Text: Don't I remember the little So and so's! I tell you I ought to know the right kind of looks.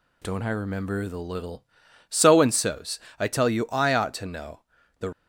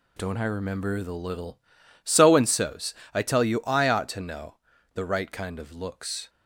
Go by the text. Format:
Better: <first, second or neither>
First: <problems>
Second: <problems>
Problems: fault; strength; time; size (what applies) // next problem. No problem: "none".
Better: second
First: pauses between "know" and "the"; at 4.6 s; 0.40 s long // stops before "right kind of looks"; at 5.1 s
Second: pauses between "know" and "the"; at 4.5 s; 0.40 s long